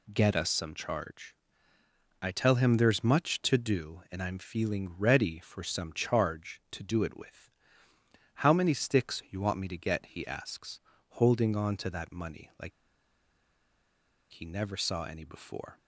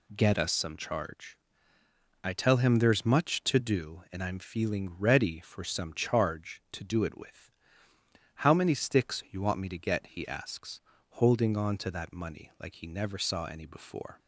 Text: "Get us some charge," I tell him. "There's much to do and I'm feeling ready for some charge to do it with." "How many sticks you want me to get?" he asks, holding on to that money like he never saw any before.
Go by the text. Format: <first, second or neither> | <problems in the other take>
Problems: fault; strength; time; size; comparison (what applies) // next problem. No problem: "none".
second | pauses between "like" and "he"; strong; at 12.7 s; 1.6 s long